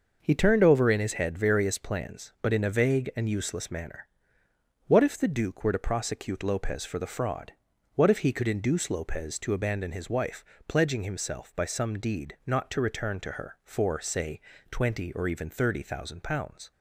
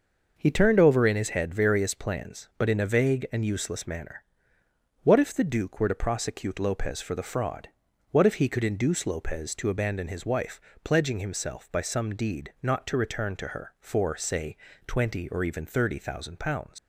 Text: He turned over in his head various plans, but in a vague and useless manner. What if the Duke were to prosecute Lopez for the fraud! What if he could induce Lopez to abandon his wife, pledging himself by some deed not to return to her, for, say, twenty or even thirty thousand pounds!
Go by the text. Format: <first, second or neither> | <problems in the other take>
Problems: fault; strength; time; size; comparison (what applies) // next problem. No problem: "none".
first | leaves "pounds" unfinished; at 16.7 s; 90 ms